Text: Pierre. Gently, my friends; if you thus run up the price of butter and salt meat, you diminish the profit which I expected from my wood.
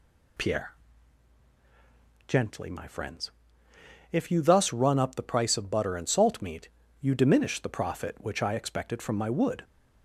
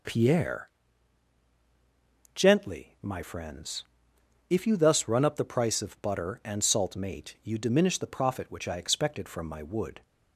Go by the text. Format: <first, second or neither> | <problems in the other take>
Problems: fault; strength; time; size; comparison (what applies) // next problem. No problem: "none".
first | says "mate" for "meat"; at 6.9 s